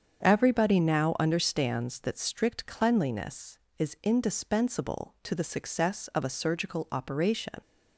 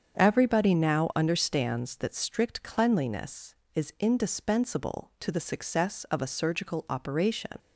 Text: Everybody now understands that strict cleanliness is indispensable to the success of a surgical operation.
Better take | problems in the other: neither | starts louder than the rest; strong; the same in both

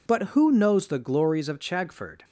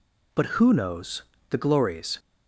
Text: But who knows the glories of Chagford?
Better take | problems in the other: first | pauses between "knows" and "the"; slight; at 1.2 s; 0.26 s long // stops before "of Chagford"; at 2.1 s

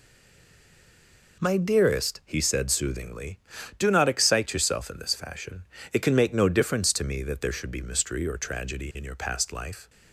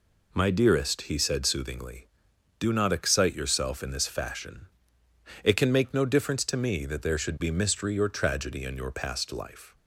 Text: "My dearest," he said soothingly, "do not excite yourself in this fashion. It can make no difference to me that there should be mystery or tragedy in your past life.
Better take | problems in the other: second | stays silent before the first word; noticeable; until 1.4 s; 1.4 s long

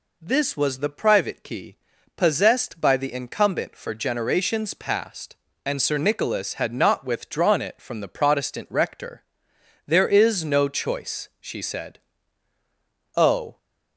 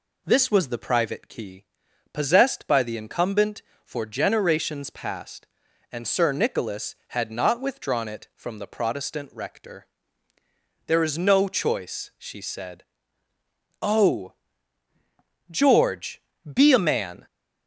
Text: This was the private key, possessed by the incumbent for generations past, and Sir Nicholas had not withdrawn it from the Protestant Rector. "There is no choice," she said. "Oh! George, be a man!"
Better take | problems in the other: second | stops before "George be a man"; at 13.5 s

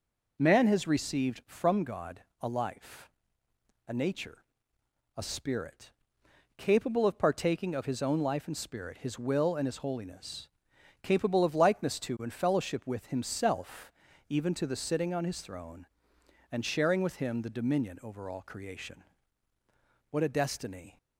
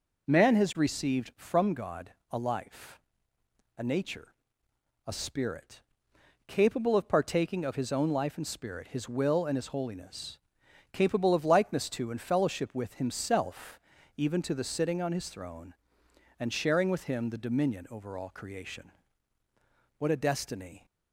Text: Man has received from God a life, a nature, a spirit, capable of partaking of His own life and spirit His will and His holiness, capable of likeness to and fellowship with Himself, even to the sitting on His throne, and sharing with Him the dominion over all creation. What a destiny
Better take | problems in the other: neither | pauses between "God" and "a"; slight; the same in both

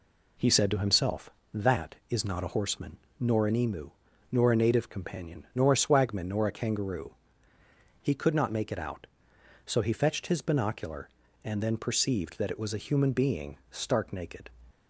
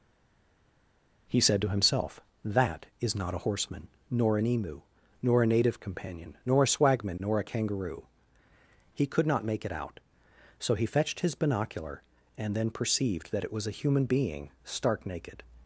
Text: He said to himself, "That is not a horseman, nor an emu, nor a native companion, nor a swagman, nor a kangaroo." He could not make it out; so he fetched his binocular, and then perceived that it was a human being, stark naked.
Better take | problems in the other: first | stays silent before the first word; noticeable; until 1.2 s; 1.2 s long

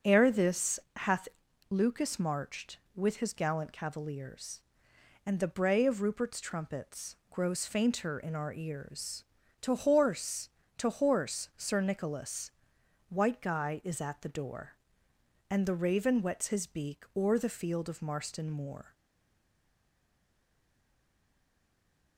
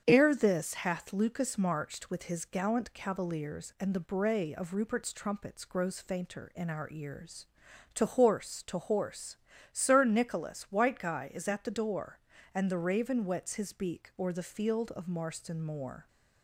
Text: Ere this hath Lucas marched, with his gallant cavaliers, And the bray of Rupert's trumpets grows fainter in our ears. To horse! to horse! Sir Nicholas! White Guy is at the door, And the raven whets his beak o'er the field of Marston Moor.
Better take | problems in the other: second | starts louder than the rest; until 1.2 s; 6.5 dB; strong in the second // pauses between "this" and "hath"; slight; at 0.7 s; 0.16 s long // pauses between "hath" and "Lucas"; at 1.2 s; 0.42 s long // pauses between "trumpets" and "grows"; slight; at 7.1 s; 0.16 s long // stays silent after the last word; strong; from 18.9 s on; 3.2 s long

